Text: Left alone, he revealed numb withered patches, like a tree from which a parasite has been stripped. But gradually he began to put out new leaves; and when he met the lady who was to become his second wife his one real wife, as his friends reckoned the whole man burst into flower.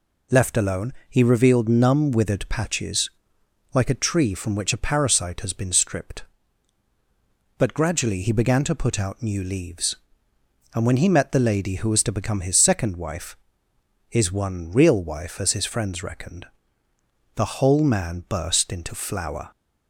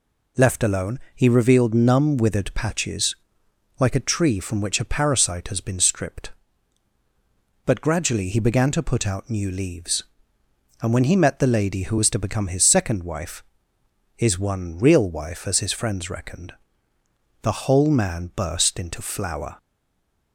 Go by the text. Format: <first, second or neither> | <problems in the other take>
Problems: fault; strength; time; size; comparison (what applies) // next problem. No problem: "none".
first | pauses between "wife" and "his"; noticeable; at 13.4 s; 0.72 s long; noticeable in the first // pauses between "reckoned" and "the"; noticeable; at 16.5 s; 0.88 s long; noticeable in the first // stays silent after the last word; slight; from 19.5 s on; 0.8 s long